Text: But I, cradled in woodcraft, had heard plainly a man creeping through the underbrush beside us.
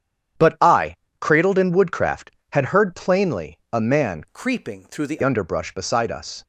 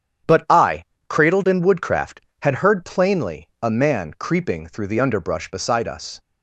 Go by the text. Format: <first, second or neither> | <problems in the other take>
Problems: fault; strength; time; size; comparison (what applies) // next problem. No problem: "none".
second | starts louder than the rest; strong; until 1.6 s; 9.5 dB; strong in the second // changes voice from "creeping" to "the"; from 4.3 to 5.1 s; 0.8 s long